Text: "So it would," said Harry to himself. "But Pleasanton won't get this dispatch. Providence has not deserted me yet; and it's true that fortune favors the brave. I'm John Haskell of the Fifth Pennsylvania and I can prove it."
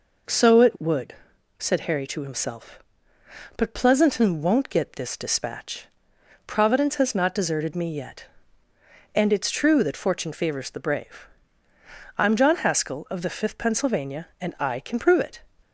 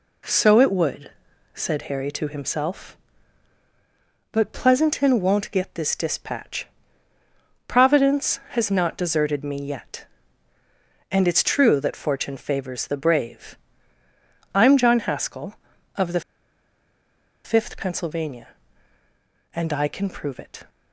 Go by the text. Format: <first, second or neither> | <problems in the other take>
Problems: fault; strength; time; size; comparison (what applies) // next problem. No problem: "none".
first | pauses between "the" and "Fifth"; at 16.2 s; 1.2 s long